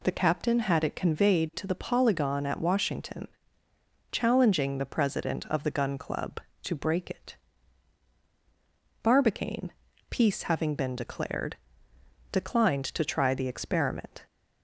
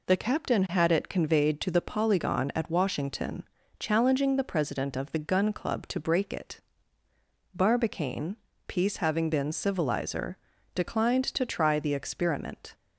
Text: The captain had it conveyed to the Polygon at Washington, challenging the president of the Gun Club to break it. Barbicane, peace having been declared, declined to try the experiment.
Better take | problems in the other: first | says "civilizer" for "declared"; at 9.5 s

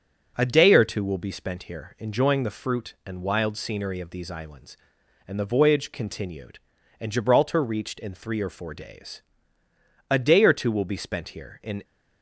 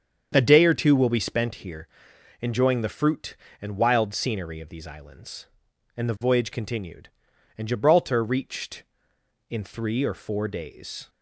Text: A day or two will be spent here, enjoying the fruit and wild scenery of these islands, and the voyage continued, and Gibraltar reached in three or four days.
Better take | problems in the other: second | starts louder than the rest; until 1.3 s; 6.5 dB; strong in the second // goes on to say "A day or two will be spent here in"; strong; from 10.0 s on; 1.7 s long

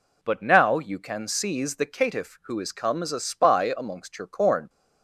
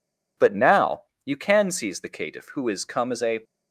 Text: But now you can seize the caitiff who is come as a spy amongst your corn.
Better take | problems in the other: first | pauses between "now" and "you"; slight; at 1.0 s; 0.22 s long // stops before "spy amongst your corn"; at 3.4 s

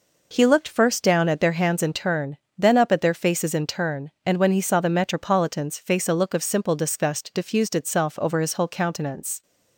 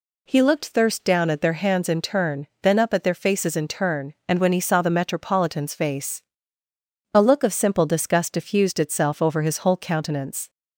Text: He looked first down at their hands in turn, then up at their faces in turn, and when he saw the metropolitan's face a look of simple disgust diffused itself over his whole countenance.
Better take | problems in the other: first | says "thirst" for "first"; at 0.6 s // pauses between "face" and "a"; noticeable; at 6.2 s; 0.92 s long

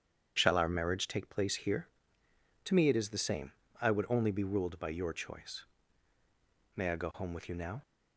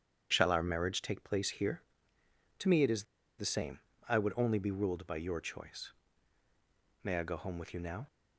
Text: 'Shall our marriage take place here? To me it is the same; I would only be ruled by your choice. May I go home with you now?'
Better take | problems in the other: first | starts louder than the rest; strong; until 1.3 s; 8.5 dB; strong in the first // pauses between "is" and "the"; slight; at 3.0 s; 0.35 s long

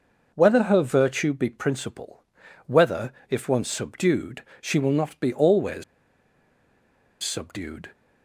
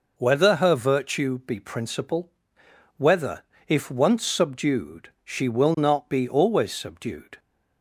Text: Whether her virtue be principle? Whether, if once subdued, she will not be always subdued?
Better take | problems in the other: second | pauses between "always" and "subdued"; strong; at 5.8 s; 1.3 s long

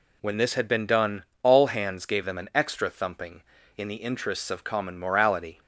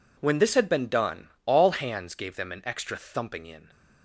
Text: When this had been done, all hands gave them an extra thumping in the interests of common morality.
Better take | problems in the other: first | stops before "the interests of common morality"; at 3.6 s

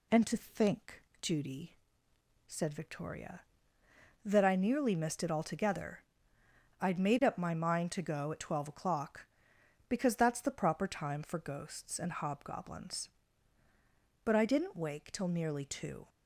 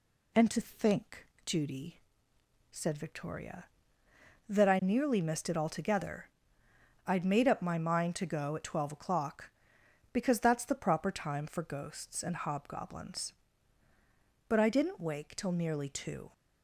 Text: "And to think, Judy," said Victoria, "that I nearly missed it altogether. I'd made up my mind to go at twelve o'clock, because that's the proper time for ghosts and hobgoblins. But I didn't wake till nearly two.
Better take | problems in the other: neither | none

